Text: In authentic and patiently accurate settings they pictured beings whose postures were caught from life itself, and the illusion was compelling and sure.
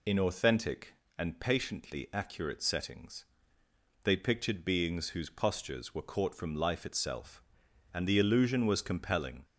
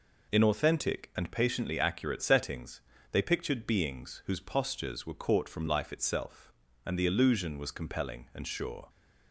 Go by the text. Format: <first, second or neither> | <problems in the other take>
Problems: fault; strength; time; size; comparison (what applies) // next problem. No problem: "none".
second | pauses between "settings" and "they"; noticeable; at 3.2 s; 0.78 s long; slight in the second // stops before "and sure"; at 9.4 s